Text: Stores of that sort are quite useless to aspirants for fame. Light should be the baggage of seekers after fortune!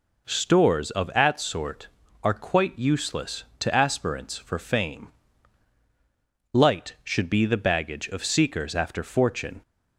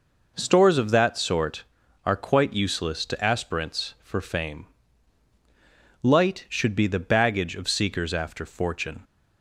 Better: second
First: says "at" for "that"; at 1.0 s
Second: none

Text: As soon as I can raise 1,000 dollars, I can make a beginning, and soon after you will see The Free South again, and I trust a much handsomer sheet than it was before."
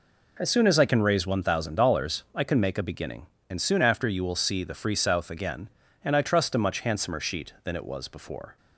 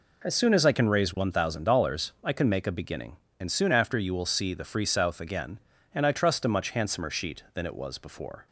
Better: neither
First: none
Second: none

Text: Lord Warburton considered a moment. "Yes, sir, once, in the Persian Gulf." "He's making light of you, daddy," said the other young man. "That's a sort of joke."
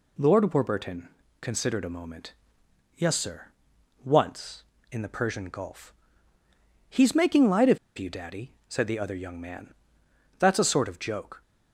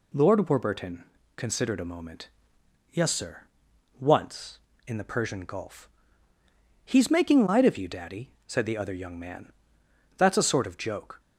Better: second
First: pauses between "Warburton" and "considered"; slight; at 1.0 s; 0.32 s long // pauses between "of" and "you"; slight; at 7.7 s; 0.20 s long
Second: pauses between "Warburton" and "considered"; slight; at 1.0 s; 0.32 s long

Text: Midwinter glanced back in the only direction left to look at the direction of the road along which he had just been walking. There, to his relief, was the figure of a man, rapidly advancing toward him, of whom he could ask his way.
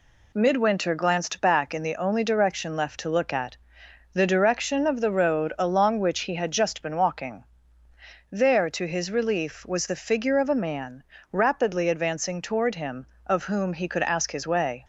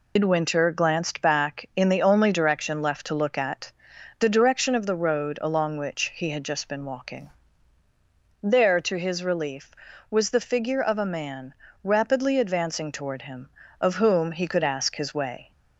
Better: first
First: pauses between "at" and "the"; noticeable; at 3.5 s; 0.56 s long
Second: loses the start of "Midwinter"; at 0.1 s; 125 ms // pauses between "at" and "the"; noticeable; at 3.7 s; 0.48 s long

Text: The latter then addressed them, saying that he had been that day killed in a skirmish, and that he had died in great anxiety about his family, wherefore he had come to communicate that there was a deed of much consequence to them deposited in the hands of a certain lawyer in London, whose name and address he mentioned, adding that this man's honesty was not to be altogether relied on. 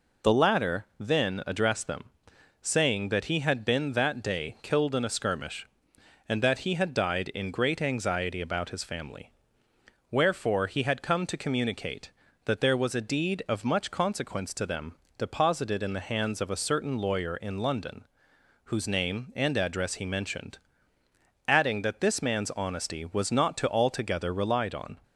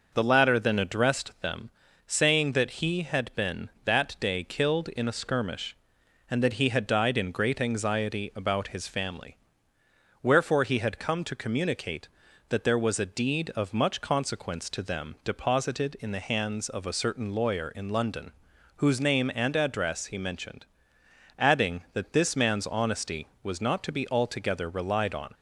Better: second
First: pauses between "them" and "deposited"; slight; at 14.9 s; 0.22 s long // skips "be"; at 23.6 s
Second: none

